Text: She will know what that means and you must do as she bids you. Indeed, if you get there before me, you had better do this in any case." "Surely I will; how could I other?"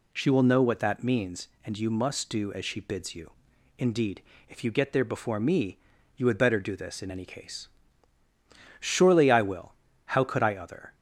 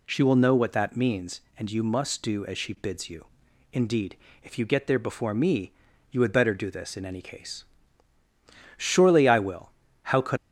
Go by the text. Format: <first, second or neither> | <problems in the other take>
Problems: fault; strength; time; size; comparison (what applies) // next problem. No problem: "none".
first | stops before "I other"; at 10.3 s